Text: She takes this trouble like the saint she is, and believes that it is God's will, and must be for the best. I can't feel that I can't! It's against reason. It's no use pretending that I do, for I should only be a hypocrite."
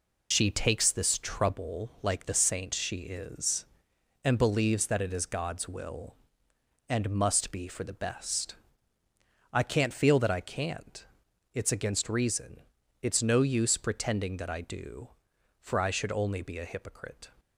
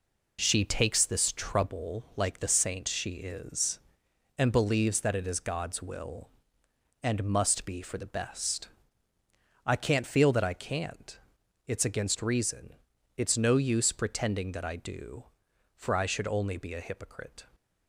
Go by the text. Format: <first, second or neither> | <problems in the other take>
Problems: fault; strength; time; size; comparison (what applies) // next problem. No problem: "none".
second | loses the start of "She"; at 0.3 s; 60 ms